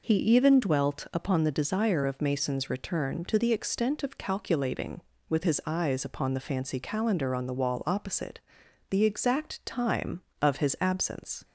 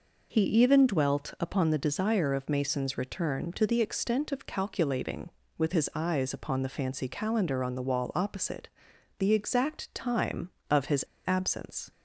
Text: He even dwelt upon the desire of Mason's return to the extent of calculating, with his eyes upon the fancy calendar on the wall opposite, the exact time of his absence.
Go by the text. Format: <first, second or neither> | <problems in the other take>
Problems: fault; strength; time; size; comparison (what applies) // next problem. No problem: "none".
first | pauses between "his" and "absence"; slight; at 11.0 s; 0.23 s long